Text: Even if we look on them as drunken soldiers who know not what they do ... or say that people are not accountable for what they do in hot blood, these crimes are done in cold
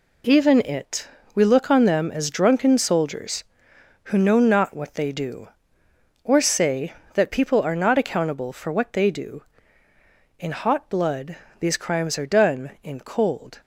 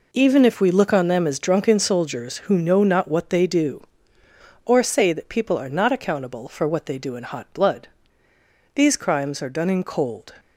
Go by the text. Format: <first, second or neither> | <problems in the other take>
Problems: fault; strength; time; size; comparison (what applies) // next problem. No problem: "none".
second | says "it" for "if"; at 0.6 s